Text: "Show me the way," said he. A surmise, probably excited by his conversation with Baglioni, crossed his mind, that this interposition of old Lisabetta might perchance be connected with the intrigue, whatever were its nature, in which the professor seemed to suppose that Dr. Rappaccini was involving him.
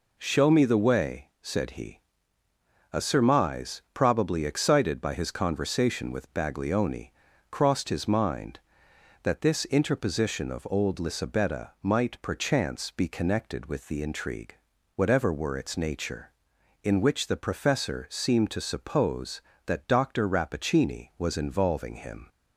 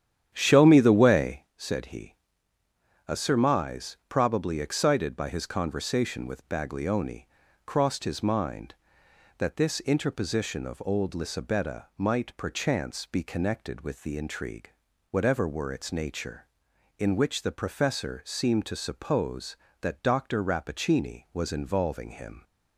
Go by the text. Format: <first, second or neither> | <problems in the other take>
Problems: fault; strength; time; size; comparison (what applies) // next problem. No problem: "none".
first | starts louder than the rest; strong; until 1.5 s; 10 dB